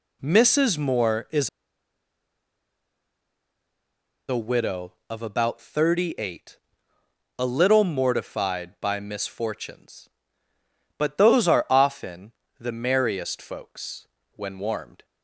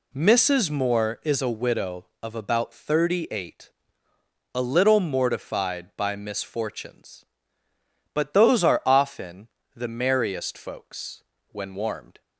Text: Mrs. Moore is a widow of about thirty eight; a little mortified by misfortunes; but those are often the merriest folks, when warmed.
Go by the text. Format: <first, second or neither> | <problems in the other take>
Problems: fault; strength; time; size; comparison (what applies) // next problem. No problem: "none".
second | pauses between "is" and "a"; strong; at 1.4 s; 2.8 s long // pauses between "often" and "the"; slight; at 12.3 s; 0.26 s long; slight in the second